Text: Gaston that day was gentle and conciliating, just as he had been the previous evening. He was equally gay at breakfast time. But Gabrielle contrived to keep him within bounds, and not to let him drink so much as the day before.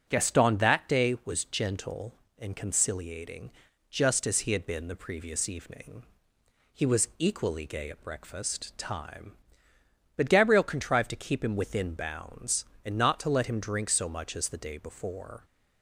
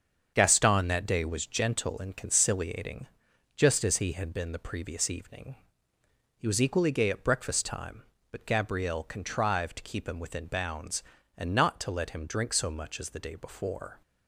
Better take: neither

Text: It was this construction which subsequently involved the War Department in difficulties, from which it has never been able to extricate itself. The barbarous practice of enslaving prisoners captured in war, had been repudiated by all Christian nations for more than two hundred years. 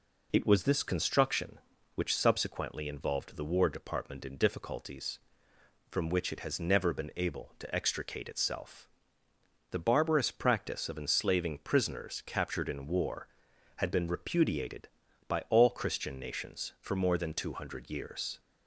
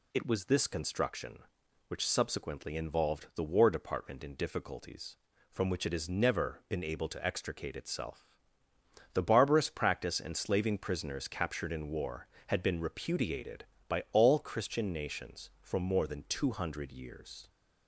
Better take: first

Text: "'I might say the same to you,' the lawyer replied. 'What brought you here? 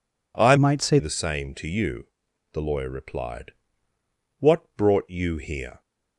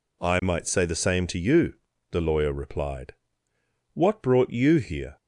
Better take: second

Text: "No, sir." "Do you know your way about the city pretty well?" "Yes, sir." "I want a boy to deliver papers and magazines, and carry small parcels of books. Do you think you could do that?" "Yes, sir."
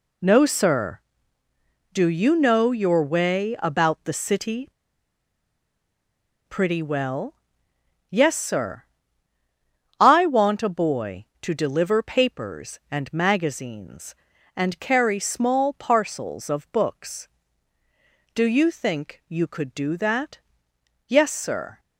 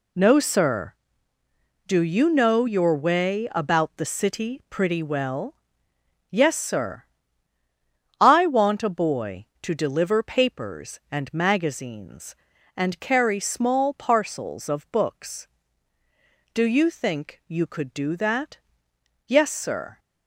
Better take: second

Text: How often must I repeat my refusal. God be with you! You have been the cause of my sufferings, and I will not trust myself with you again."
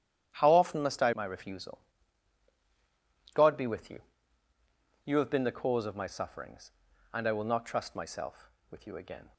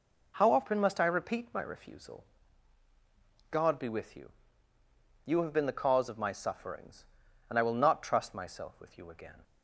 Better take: second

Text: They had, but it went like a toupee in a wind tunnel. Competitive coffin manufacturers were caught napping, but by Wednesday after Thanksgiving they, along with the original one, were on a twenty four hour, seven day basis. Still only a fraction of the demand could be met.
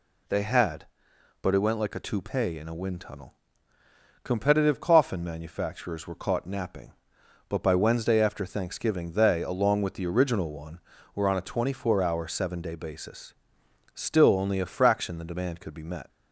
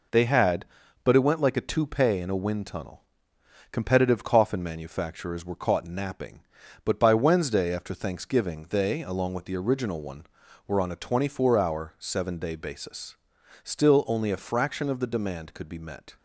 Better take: second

